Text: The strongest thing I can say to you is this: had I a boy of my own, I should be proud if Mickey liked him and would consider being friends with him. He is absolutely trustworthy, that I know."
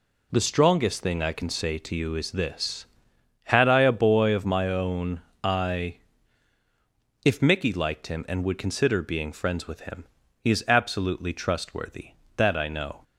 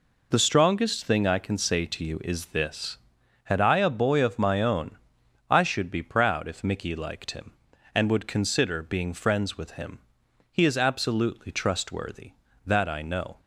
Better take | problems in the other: second | skips "should be proud"; at 6.6 s

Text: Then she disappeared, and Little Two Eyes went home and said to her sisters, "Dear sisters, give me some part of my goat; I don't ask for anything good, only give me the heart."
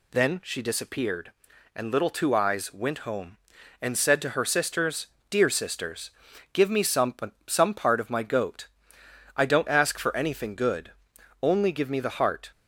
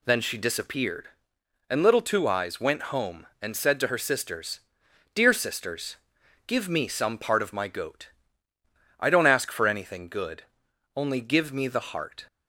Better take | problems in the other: second | says "some" twice; at 7.4 s

